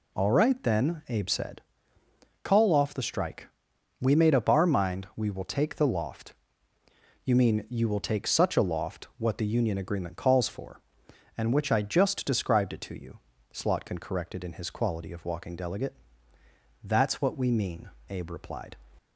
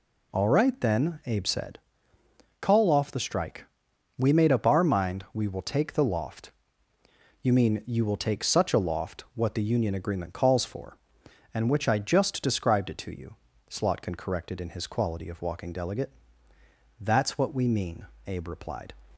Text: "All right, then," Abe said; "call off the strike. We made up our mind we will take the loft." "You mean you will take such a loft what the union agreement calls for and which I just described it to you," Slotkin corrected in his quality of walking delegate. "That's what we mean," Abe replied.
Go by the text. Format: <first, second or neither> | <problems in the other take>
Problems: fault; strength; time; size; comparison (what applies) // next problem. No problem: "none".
neither | none